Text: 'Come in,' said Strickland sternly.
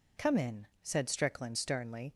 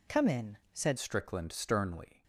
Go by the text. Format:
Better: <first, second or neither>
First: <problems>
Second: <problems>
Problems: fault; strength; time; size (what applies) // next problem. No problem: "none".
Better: first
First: none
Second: changes voice at "Strickland"; from 0.9 s on; 1.3 s long